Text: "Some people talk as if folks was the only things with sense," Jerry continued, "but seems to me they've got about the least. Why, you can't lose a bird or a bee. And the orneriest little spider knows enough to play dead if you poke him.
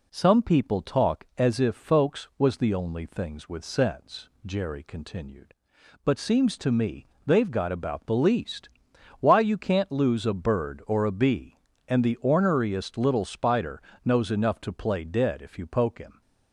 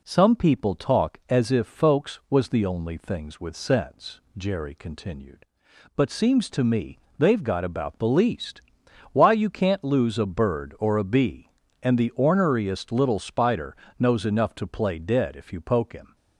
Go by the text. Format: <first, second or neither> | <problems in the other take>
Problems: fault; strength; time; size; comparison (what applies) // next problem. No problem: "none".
neither | pauses between "me" and "they've"; slight; the same in both // pauses between "spider" and "knows"; slight; the same in both